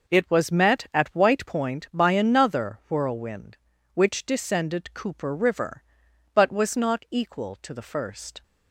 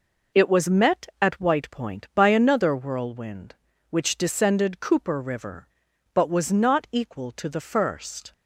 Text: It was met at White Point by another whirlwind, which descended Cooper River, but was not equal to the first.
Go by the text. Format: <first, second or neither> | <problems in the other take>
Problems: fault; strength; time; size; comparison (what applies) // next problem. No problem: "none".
neither | none